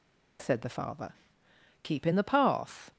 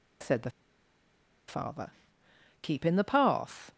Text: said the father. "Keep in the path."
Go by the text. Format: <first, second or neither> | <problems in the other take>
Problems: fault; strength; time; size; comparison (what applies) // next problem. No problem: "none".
first | pauses between "the" and "father"; at 0.4 s; 0.98 s long